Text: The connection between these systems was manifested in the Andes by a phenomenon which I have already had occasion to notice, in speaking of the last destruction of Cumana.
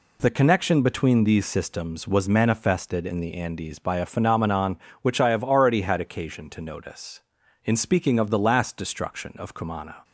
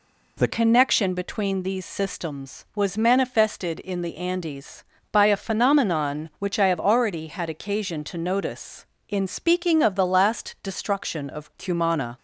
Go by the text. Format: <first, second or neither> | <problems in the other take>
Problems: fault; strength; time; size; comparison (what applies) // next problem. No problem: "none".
first | changes voice at "connection"; from 0.4 s on; 11.7 s long